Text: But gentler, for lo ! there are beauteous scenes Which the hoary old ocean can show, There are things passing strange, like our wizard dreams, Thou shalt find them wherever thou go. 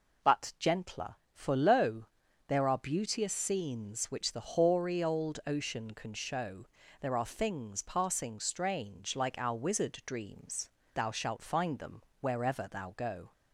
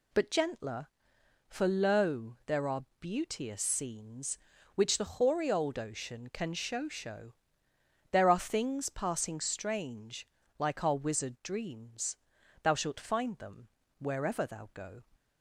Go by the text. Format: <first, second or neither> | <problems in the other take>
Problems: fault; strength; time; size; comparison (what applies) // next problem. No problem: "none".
first | pauses between "are" and "beauteous"; slight; at 2.8 s; 0.16 s long // says "show" twice; at 6.8 s // pauses between "them" and "wherever"; slight; at 13.6 s; 0.30 s long; slight in the first